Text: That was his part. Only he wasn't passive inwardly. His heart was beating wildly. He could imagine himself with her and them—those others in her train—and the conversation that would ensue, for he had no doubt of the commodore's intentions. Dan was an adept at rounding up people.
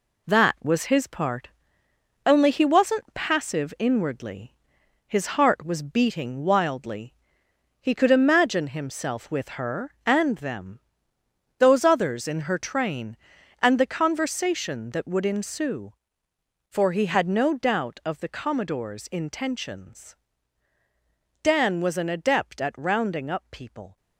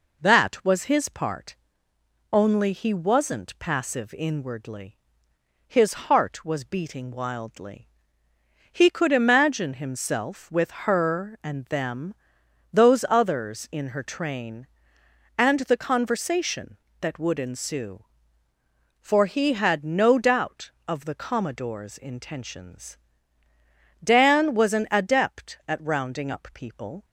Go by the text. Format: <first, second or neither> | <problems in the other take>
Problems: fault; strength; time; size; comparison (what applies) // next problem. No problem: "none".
second | gets quieter; noticeable; throughout; 5.5 dB